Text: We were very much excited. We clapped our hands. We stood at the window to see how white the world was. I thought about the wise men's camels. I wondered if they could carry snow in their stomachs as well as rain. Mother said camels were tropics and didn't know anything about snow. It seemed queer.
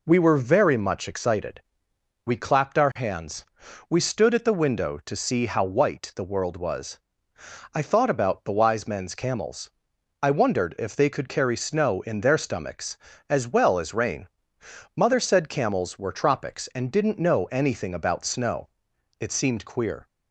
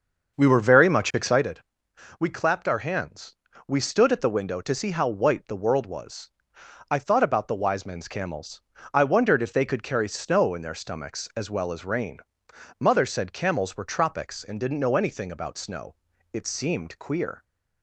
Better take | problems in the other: first | starts louder than the rest; until 1.5 s; 6.5 dB

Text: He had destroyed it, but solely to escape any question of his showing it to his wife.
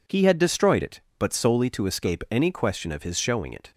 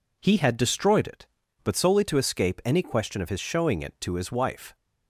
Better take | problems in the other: second | stops before "to his wife"; at 3.7 s

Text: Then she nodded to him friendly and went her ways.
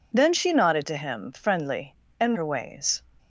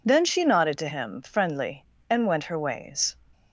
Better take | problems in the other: second | skips "went"; at 2.3 s

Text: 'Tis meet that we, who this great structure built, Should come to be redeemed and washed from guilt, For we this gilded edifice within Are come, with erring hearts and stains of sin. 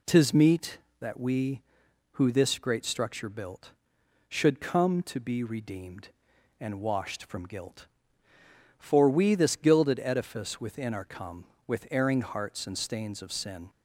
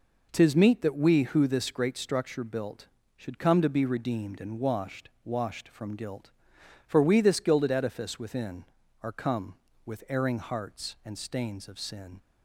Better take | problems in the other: first | says "washed" twice; at 5.2 s

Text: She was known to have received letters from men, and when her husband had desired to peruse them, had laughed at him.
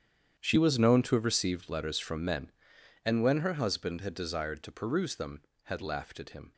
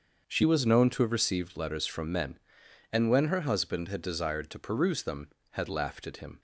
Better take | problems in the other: second | gets quieter; strong; throughout; 15.5 dB // starts louder than the rest; strong; until 1.4 s; 9 dB; also in the second

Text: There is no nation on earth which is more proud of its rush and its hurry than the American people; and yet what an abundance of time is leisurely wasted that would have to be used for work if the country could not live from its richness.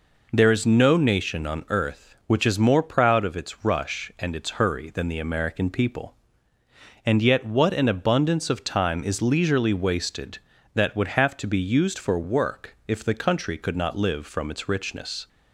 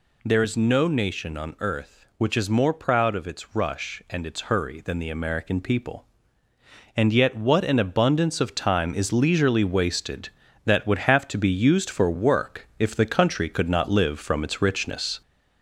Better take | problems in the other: first | gets louder; throughout; 3.5 dB

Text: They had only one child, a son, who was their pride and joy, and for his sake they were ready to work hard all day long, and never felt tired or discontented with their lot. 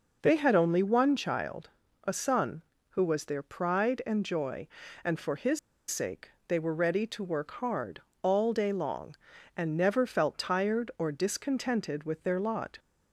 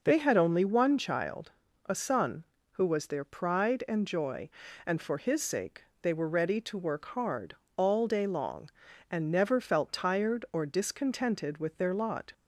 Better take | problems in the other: second | pauses between "his" and "sake"; slight; at 5.5 s; 0.31 s long // pauses between "sake" and "they"; slight; at 6.3 s; 0.16 s long; slight in the second // pauses between "hard" and "all"; slight; at 8.0 s; 0.22 s long; slight in the second

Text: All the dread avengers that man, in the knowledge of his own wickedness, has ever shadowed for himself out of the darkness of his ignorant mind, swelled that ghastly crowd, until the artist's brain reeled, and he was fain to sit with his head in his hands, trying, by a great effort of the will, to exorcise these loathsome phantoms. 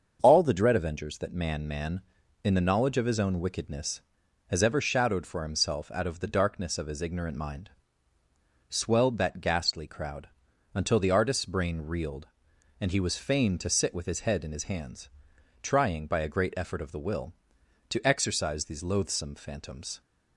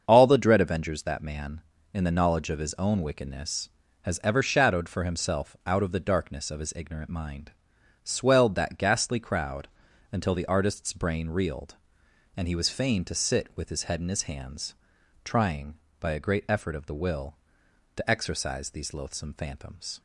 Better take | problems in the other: second | starts louder than the rest; until 1.2 s; 7 dB; also in the second // says "man" twice; at 1.6 s

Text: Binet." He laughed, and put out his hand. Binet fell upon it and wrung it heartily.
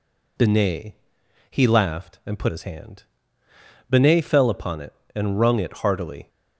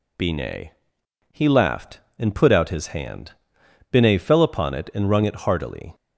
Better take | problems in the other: second | skips "out"; at 2.4 s

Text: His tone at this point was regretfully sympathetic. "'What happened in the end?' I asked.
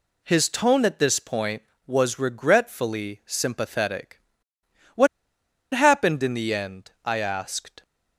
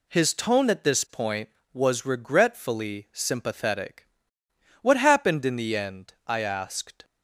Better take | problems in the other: second | pauses between "What" and "happened"; noticeable; at 5.0 s; 0.66 s long

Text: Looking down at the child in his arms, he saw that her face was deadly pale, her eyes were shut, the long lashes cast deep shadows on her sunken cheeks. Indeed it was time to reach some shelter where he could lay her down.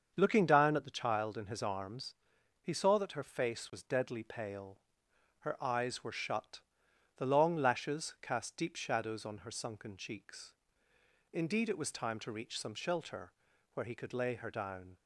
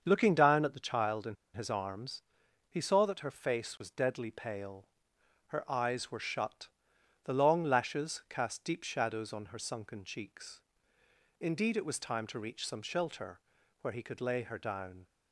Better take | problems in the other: first | starts louder than the rest; until 1.0 s; 7 dB; also in the first // pauses between "in" and "his"; slight; at 1.3 s; 0.18 s long // pauses between "shelter" and "where"; at 13.3 s; 0.40 s long; also in the first

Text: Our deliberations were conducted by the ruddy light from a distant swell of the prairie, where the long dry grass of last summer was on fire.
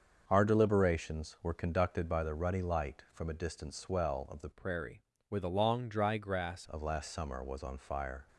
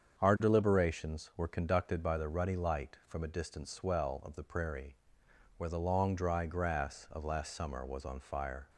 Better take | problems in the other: second | starts louder than the rest; until 1.2 s; 6.5 dB; strong in the second // changes voice from "prairie" to "grass"; from 4.5 to 6.6 s; 2.1 s long

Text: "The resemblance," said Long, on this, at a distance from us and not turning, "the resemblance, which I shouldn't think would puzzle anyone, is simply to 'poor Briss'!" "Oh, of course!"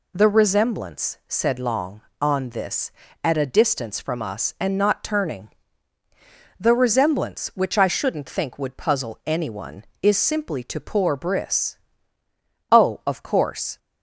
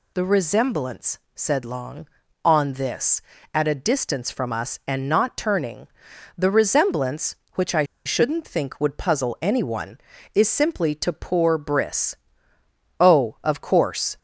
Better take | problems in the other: first | pauses between "I" and "shouldn't"; slight; at 7.8 s; 0.22 s long

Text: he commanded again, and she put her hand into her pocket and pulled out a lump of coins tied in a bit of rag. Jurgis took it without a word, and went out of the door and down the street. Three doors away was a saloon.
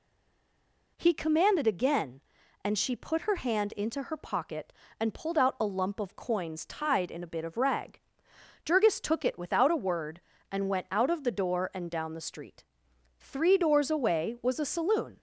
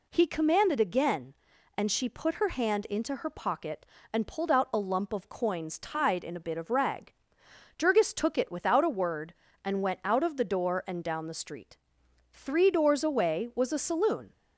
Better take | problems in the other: second | stays silent before the first word; until 0.9 s; 0.9 s long

